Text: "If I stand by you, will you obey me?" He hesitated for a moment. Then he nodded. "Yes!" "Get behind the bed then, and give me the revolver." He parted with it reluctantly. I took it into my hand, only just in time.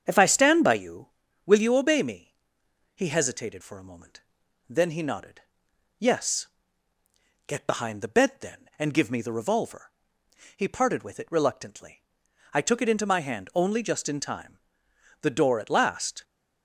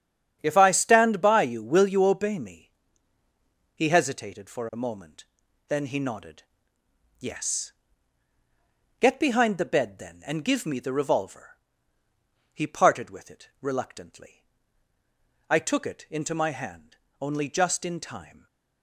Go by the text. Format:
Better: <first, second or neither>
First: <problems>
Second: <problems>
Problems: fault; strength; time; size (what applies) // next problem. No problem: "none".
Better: second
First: starts louder than the rest; strong; until 1.0 s; 7.5 dB // goes on to say "The door at last"; noticeable; from 15.2 s on; 1.0 s long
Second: starts louder than the rest; strong; until 1.4 s; 8.5 dB